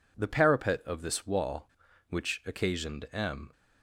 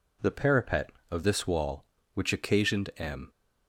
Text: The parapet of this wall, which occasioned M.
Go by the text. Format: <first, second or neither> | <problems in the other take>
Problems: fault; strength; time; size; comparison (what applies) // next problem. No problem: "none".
neither | none